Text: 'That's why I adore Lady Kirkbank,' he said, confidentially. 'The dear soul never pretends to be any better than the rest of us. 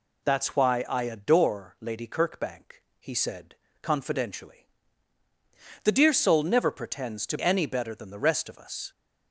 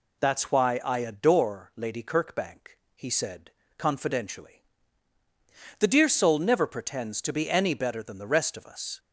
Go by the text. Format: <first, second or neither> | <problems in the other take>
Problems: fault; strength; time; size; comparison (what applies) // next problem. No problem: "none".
second | skips "be"; at 7.3 s